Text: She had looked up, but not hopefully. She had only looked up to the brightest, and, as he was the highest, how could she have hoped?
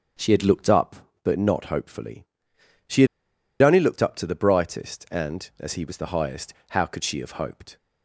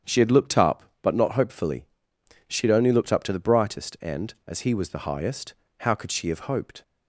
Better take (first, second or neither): second